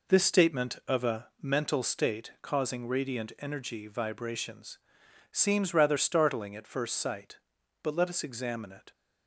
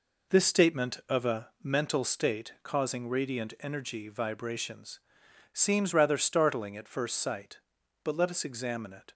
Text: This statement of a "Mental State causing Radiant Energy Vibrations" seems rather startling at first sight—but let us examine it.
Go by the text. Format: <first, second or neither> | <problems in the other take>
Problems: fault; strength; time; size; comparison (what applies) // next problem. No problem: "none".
neither | pauses between "Vibrations" and "seems"; noticeable; the same in both